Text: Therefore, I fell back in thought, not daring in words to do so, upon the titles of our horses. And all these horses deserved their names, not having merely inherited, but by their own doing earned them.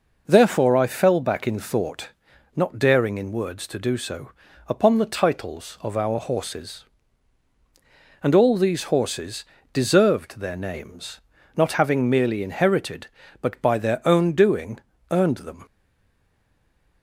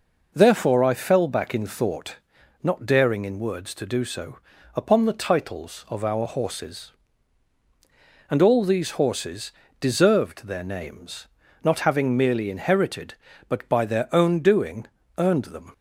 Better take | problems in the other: second | pauses between "horses" and "deserved"; slight; at 9.4 s; 0.26 s long; slight in the second // pauses between "doing" and "earned"; slight; at 14.7 s; 0.32 s long; slight in the second // stays silent after the last word; noticeable; from 15.6 s on; 1.4 s long

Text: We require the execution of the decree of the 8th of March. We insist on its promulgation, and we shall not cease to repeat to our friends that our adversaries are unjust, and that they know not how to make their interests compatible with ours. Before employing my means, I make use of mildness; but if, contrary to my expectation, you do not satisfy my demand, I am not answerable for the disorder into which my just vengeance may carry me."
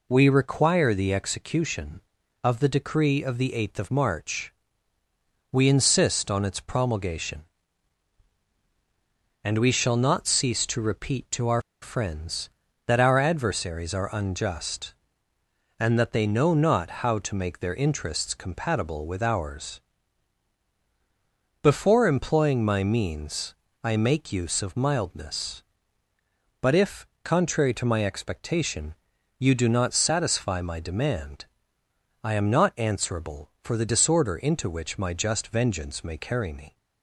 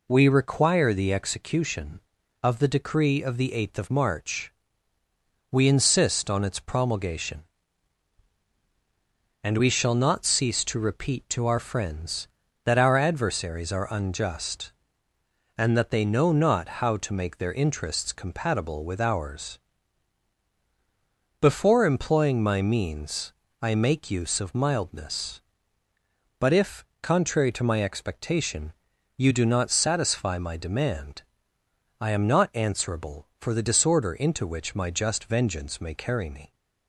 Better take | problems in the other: second | pauses between "our" and "friends"; slight; at 11.6 s; 0.21 s long // pauses between "not" and "how"; slight; at 16.9 s; 0.16 s long; slight in the second

